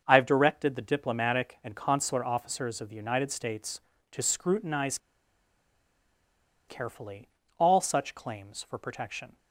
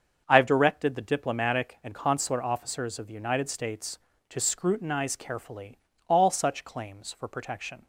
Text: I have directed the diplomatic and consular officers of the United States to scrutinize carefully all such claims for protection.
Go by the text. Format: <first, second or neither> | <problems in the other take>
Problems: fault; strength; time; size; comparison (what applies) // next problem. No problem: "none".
second | starts louder than the rest; until 1.0 s; 6.5 dB; also in the second // pauses between "scrutinize" and "carefully"; strong; at 4.9 s; 1.6 s long // pauses between "carefully" and "all"; slight; at 7.2 s; 0.30 s long; slight in the second